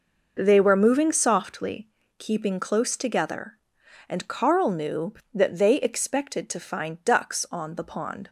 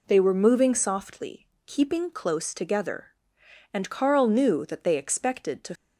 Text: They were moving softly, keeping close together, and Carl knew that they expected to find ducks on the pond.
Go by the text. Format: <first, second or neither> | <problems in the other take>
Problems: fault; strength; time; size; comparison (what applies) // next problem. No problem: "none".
first | stops before "find ducks on the pond"; at 5.7 s